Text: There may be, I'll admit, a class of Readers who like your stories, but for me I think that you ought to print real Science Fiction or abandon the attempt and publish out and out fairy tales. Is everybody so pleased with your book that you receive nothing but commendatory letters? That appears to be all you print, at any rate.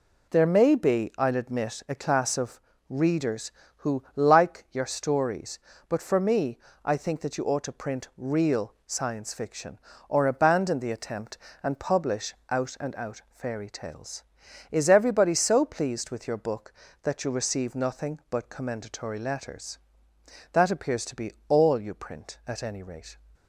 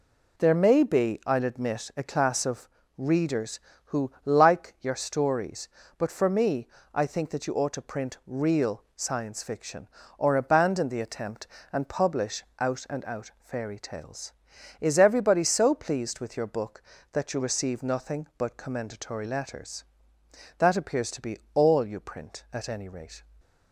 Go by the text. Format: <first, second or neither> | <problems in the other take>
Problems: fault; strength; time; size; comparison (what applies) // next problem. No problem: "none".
neither | pauses between "of" and "Readers"; slight; the same in both // pauses between "me" and "I"; slight; the same in both // pauses between "publish" and "out"; slight; the same in both // pauses between "be" and "all"; slight; the same in both